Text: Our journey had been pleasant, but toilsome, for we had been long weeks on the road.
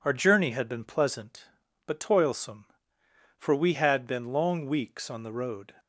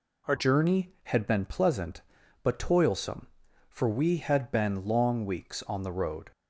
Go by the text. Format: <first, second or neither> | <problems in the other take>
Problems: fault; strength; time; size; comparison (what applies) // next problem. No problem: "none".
first | changes voice at "journey"; from 0.3 s on; 6.0 s long